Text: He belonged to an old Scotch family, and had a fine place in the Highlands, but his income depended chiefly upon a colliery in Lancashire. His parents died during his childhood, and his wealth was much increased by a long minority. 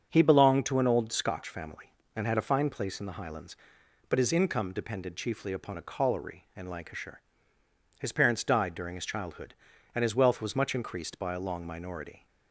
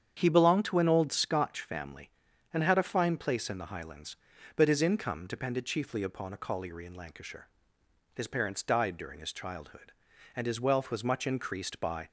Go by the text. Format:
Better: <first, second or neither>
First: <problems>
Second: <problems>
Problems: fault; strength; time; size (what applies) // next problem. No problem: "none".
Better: first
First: starts louder than the rest; strong; until 1.1 s; 7 dB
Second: starts louder than the rest; strong; until 1.1 s; 8 dB // stops before "a long minority"; at 12.0 s